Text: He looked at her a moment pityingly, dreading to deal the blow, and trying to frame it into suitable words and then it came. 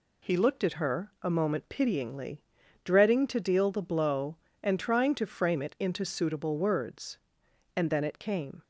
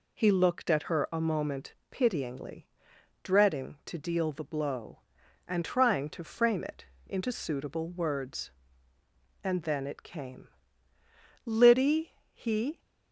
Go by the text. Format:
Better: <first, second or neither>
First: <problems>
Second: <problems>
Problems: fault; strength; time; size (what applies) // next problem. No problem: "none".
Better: first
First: none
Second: pauses between "moment" and "pityingly"; slight; at 1.7 s; 0.16 s long // pauses between "it" and "into"; slight; at 6.8 s; 0.20 s long // goes on to say "Liddy he"; from 11.4 s on; 1.3 s long